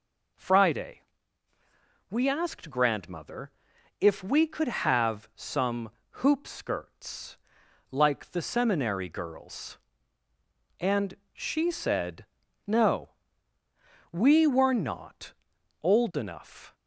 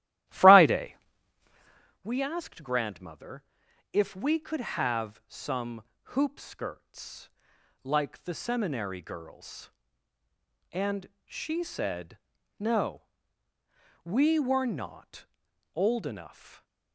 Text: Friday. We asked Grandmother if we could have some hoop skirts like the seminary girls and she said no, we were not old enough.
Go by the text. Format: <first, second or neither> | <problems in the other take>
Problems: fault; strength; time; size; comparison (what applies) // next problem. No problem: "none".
first | starts louder than the rest; strong; until 2.0 s; 14 dB // pauses between "Grandmother" and "if"; noticeable; at 3.4 s; 0.48 s long; noticeable in the first // pauses between "some" and "hoop"; slight; at 5.8 s; 0.32 s long; slight in the first // pauses between "skirts" and "like"; noticeable; at 7.2 s; 0.54 s long; noticeable in the first // pauses between "and" and "she"; slight; at 11.0 s; 0.16 s long; slight in the first // pauses between "said" and "no"; at 12.1 s; 0.40 s long; also in the first // pauses between "not" and "old"; noticeable; at 15.2 s; 0.48 s long; noticeable in the first